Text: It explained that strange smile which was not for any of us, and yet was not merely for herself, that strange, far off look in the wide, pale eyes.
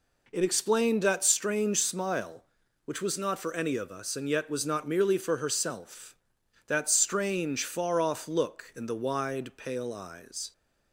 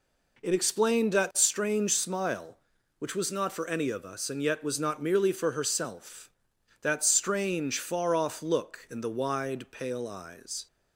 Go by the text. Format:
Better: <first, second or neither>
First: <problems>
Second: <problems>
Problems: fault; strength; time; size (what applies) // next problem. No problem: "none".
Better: neither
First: none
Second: none